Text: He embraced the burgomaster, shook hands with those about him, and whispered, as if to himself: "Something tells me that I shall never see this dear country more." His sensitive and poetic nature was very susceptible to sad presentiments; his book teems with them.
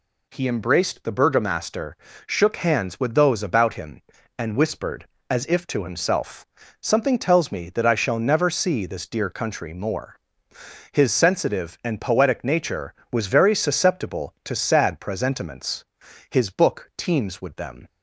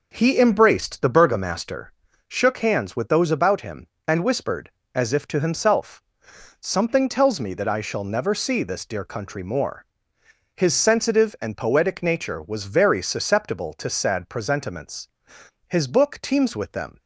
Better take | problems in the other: first | starts louder than the rest; noticeable; until 1.8 s; 5 dB

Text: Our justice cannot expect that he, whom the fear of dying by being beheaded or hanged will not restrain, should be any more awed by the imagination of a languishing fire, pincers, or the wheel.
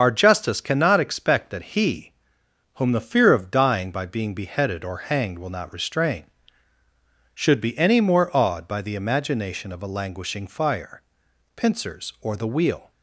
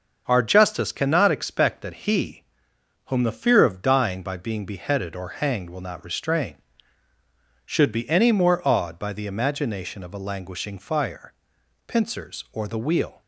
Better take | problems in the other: second | loses the start of "Our"; at 0.0 s; 45 ms // starts louder than the rest; until 1.0 s; 7 dB; also in the second

